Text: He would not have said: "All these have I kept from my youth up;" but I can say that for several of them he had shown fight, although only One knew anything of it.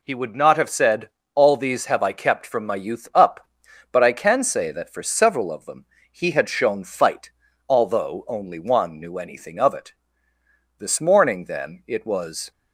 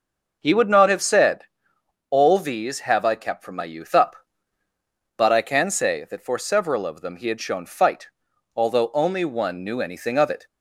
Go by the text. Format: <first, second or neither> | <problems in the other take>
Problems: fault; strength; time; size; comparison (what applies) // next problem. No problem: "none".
second | pauses between "them" and "he"; slight; at 5.8 s; 0.26 s long // goes on to say "This morning then it was"; strong; from 10.7 s on; 1.7 s long